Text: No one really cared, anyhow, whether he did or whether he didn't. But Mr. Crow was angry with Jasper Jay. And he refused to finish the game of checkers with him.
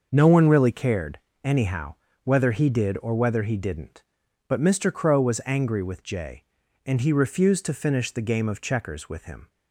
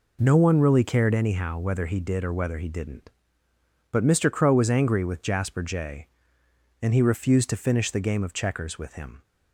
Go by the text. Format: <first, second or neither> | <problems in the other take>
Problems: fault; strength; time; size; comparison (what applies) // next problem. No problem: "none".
second | starts louder than the rest; until 1.1 s; 6 dB // skips "Jasper"; at 6.0 s